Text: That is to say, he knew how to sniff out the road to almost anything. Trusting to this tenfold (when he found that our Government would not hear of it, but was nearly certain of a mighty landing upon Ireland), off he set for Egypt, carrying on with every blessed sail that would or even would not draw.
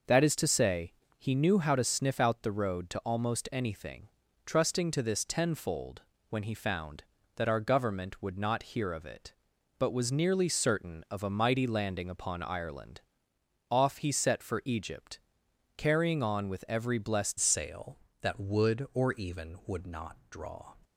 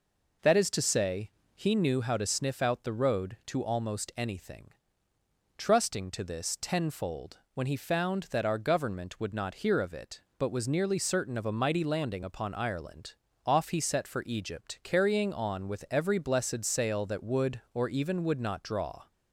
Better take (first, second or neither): second